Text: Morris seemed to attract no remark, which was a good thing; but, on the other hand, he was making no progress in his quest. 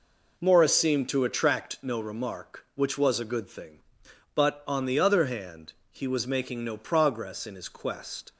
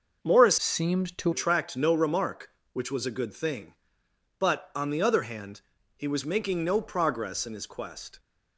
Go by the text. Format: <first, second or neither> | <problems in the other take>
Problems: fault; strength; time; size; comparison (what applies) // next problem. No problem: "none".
first | changes voice from "seemed" to "to"; from 0.5 to 1.3 s; 0.8 s long